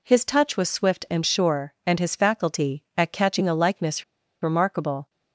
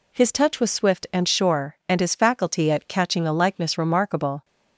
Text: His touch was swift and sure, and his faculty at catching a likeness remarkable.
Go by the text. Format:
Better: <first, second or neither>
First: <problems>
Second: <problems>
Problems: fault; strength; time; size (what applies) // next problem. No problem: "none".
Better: second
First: pauses between "likeness" and "remarkable"; at 4.0 s; 0.38 s long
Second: none